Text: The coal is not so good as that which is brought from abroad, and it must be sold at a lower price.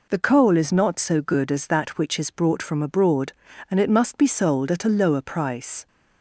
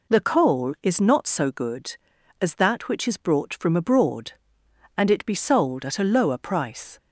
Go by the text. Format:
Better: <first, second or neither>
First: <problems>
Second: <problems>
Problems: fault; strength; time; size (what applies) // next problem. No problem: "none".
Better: first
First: none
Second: skips "must"; at 5.2 s